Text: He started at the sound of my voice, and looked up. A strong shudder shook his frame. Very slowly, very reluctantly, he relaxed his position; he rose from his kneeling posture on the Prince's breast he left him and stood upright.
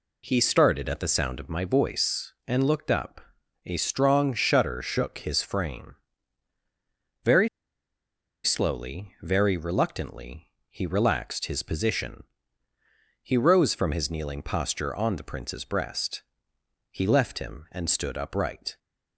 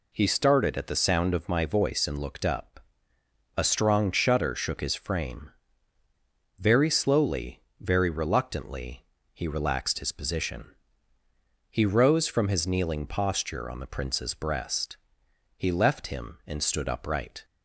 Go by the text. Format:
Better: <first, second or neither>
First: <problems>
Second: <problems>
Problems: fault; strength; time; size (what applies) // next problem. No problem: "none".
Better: second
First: pauses between "Very" and "slowly"; noticeable; at 7.4 s; 0.97 s long // pauses between "breast" and "he"; noticeable; at 16.2 s; 0.68 s long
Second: pauses between "breast" and "he"; noticeable; at 14.9 s; 0.62 s long